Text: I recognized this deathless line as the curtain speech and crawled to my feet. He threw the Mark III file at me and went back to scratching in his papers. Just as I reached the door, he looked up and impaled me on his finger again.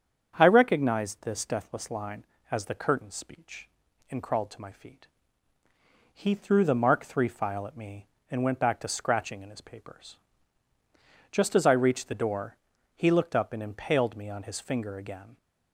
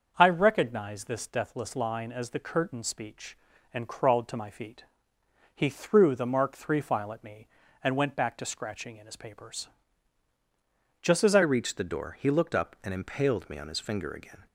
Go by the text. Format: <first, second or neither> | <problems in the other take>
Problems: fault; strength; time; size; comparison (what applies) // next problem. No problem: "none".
first | starts louder than the rest; until 1.1 s; 6.5 dB; strong in the first // changes voice at "reached"; from 11.4 s on; 3.0 s long